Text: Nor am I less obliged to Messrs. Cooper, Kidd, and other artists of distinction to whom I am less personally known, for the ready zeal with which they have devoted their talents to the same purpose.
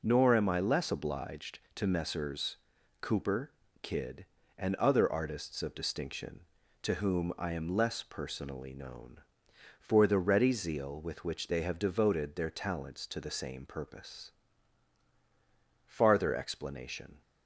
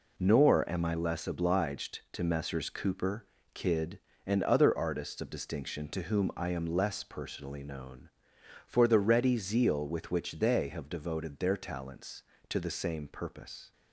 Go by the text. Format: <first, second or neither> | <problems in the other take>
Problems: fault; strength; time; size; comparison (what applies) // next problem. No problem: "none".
second | pauses between "Messrs" and "Cooper"; at 2.5 s; 0.42 s long // goes on to say "Farther explanation"; from 15.8 s on; 1.3 s long